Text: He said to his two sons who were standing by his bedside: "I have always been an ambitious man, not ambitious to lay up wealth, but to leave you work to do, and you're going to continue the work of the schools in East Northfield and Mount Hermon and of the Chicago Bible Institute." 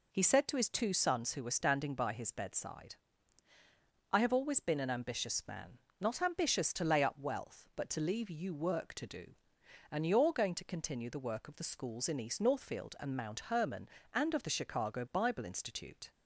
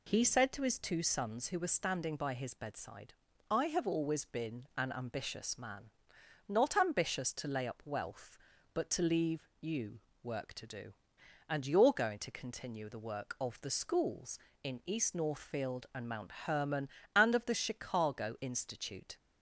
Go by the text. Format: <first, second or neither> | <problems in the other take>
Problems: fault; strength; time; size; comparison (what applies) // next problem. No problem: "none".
first | pauses between "you" and "work"; slight; at 9.9 s; 0.24 s long // pauses between "Mount" and "Hermon"; slight; at 16.2 s; 0.16 s long // skips "Bible"; at 18.3 s